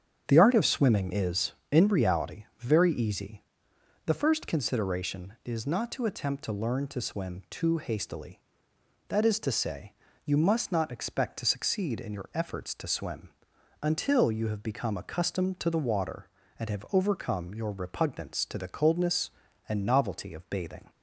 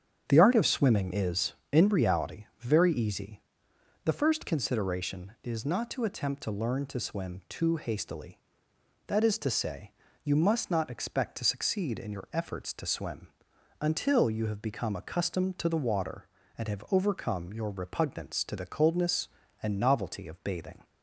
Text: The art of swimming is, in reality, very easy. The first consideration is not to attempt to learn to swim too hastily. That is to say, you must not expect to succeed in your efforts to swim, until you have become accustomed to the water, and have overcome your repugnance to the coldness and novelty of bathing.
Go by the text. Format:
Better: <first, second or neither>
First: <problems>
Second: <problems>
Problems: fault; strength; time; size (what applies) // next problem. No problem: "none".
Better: neither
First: starts louder than the rest; strong; until 1.2 s; 8 dB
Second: starts louder than the rest; strong; until 1.2 s; 8 dB